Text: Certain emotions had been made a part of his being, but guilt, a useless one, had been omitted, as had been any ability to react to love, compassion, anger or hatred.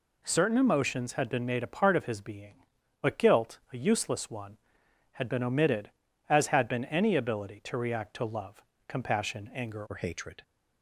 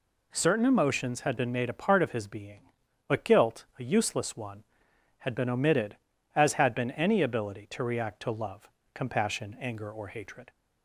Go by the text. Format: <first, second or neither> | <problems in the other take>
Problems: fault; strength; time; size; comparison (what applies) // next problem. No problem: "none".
second | changes voice at "or"; from 9.8 s on; 0.6 s long